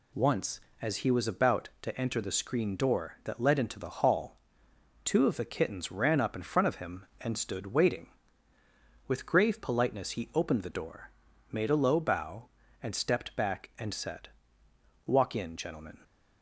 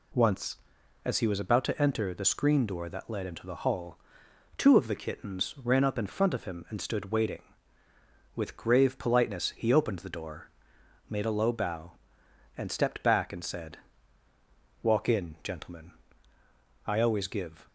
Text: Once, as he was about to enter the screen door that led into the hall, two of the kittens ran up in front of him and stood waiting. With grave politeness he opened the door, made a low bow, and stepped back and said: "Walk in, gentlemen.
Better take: first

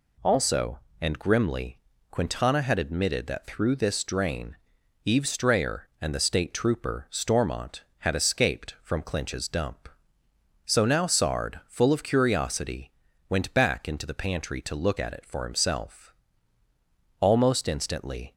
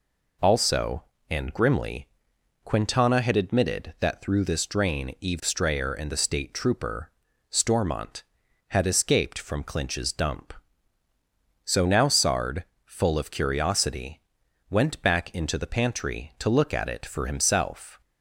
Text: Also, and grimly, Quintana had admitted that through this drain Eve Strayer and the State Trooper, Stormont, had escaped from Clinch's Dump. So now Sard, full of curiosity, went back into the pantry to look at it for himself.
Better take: second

